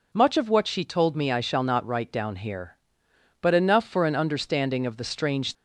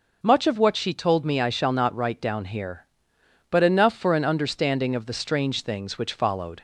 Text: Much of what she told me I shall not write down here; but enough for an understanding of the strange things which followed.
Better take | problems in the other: second | stops before "things which followed"; at 5.5 s

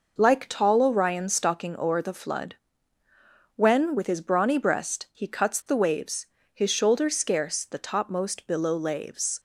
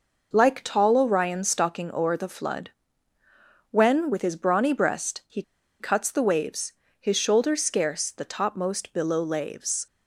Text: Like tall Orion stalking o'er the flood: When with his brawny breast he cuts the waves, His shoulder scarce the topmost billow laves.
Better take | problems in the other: first | pauses between "he" and "cuts"; at 5.4 s; 0.37 s long

